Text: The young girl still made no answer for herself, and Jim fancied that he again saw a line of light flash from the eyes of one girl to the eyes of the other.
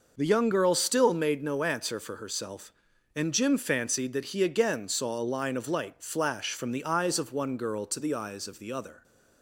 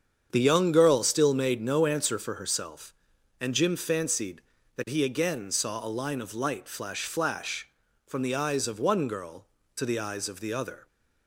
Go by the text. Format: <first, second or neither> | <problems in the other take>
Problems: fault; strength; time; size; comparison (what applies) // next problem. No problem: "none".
first | starts louder than the rest; strong; until 1.3 s; 7.5 dB // says "flash" twice; at 7.0 s